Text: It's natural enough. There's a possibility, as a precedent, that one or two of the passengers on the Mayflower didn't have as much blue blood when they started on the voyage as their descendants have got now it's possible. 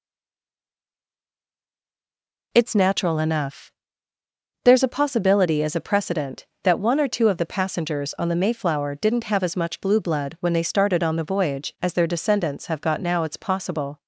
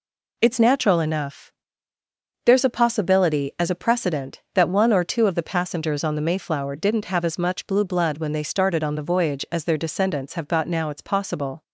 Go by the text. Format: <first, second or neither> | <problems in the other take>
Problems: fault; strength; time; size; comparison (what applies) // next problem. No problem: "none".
second | stays silent before the first word; strong; until 2.5 s; 2.5 s long